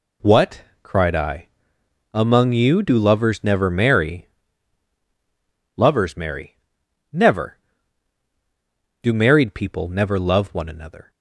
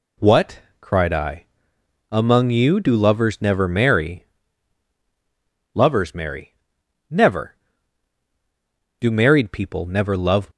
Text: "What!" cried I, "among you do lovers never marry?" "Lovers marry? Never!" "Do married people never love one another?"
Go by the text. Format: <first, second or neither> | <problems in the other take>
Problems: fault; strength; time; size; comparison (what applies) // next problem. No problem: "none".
first | stops before "one another"; at 10.5 s